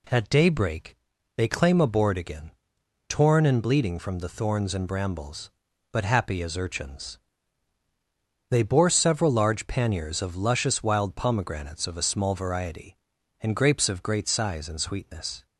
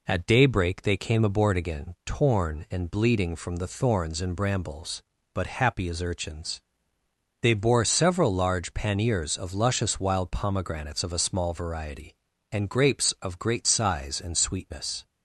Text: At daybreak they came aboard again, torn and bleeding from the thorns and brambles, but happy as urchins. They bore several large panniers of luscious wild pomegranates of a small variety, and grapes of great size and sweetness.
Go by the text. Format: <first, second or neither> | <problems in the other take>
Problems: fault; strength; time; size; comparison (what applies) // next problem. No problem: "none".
second | pauses between "daybreak" and "they"; at 0.9 s; 0.40 s long // says "claim" for "came"; at 1.4 s